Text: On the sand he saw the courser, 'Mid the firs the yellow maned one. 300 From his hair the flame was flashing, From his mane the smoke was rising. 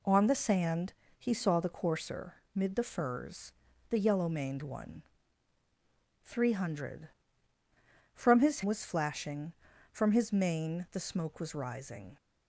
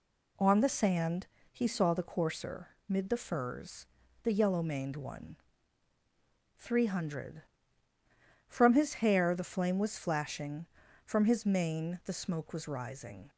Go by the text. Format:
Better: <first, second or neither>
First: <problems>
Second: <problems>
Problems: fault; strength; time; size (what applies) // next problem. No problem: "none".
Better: second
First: pauses between "sand" and "he"; slight; at 0.9 s; 0.24 s long // pauses between "firs" and "the"; at 3.5 s; 0.38 s long // skips "hair the flame"; at 8.6 s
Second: pauses between "sand" and "he"; slight; at 1.2 s; 0.24 s long // pauses between "firs" and "the"; at 3.8 s; 0.38 s long